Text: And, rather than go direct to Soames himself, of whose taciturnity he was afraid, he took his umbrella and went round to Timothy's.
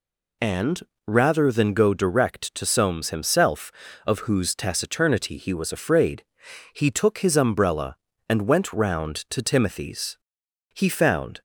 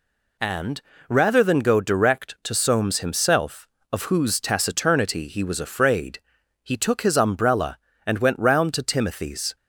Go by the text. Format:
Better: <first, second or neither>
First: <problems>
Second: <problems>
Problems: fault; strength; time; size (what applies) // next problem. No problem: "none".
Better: second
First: goes on to say "He found"; noticeable; from 10.7 s on; 0.68 s long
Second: none